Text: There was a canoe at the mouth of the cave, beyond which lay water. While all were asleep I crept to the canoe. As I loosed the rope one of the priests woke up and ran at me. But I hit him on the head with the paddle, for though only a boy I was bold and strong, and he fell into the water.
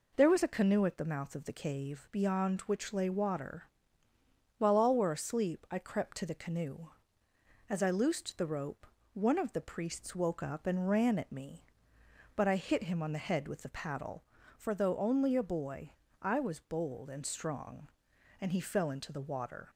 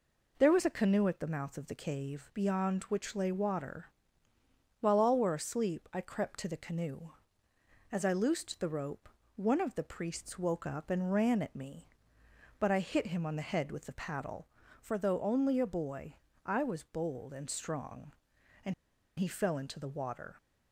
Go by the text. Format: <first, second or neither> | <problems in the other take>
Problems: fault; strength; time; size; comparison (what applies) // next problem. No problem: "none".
first | pauses between "rope" and "one"; slight; at 9.0 s; 0.30 s long; slight in the first // pauses between "boy" and "I"; slight; at 16.1 s; 0.28 s long; slight in the first // pauses between "and" and "he"; noticeable; at 18.7 s; 0.46 s long